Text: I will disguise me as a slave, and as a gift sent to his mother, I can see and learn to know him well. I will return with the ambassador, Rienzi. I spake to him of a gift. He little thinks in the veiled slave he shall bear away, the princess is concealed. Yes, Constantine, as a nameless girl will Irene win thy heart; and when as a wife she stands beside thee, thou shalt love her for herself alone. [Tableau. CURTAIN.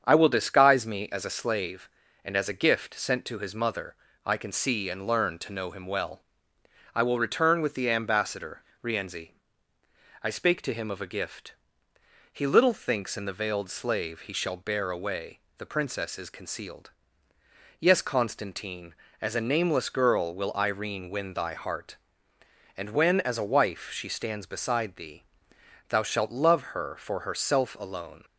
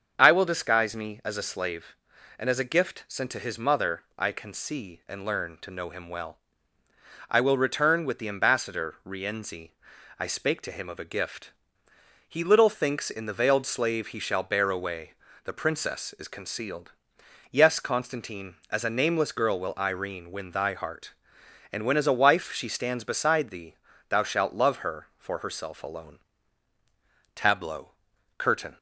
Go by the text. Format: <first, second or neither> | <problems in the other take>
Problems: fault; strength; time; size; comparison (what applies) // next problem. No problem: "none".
second | starts louder than the rest; strong; until 1.0 s; 7 dB; also in the second // stops before "Tableau CURTAIN"; at 28.2 s